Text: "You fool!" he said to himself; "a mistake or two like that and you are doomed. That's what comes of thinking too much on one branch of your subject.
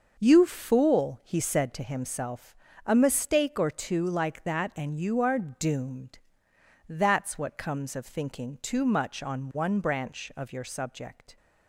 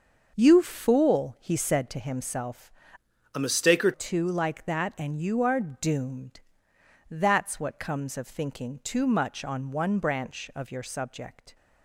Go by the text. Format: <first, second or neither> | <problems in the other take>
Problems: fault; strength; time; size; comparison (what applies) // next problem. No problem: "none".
first | starts louder than the rest; until 1.3 s; 6 dB; noticeable in the first // changes voice from "a" to "or"; from 3.3 to 3.9 s; 0.6 s long